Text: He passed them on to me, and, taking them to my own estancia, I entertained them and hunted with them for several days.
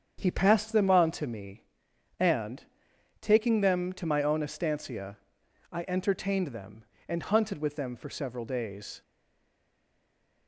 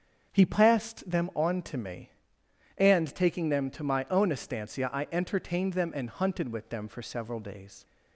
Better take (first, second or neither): second